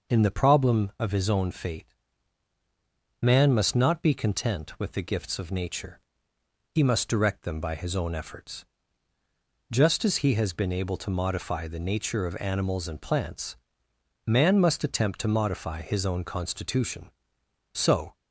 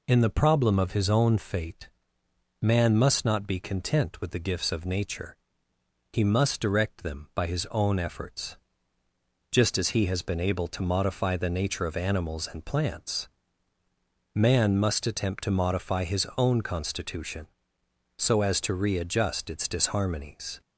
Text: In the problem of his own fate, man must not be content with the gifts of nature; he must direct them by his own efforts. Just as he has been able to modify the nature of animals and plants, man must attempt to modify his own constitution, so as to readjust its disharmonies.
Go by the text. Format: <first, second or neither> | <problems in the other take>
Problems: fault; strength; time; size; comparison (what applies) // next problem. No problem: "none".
second | stops before "as to readjust its disharmonies"; at 18.1 s